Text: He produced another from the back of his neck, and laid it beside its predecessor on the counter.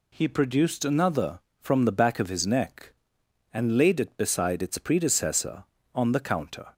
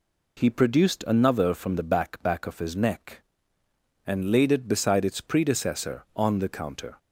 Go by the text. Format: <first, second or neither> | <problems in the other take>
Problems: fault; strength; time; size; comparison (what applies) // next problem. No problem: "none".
first | says "back" twice; at 2.2 s